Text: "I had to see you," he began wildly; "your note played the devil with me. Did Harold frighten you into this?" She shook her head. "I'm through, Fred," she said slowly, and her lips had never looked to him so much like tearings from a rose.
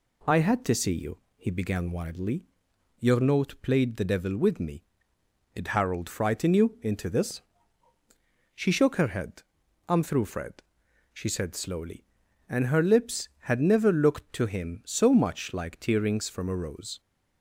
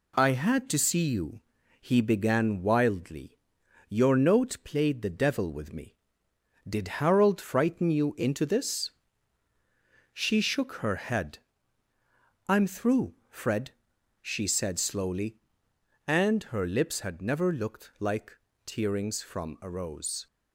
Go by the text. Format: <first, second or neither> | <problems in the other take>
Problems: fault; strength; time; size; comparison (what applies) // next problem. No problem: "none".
first | skips "to him so much"; at 17.9 s // pauses between "like" and "tearings"; slight; at 18.3 s; 0.28 s long